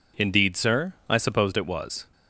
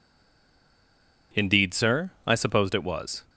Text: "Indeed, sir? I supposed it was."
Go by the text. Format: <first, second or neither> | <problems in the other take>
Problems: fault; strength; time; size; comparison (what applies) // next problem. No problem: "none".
first | stays silent before the first word; noticeable; until 1.3 s; 1.3 s long